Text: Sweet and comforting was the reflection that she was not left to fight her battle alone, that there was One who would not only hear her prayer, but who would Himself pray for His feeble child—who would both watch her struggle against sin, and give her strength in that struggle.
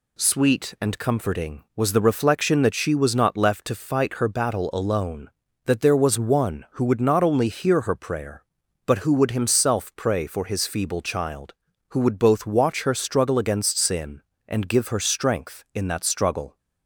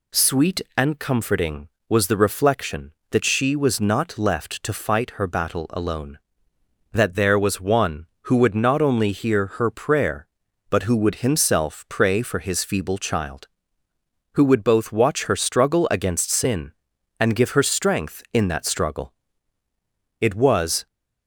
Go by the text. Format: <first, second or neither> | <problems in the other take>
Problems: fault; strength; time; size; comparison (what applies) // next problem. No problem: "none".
first | goes on to say "It was"; noticeable; from 20.1 s on; 0.66 s long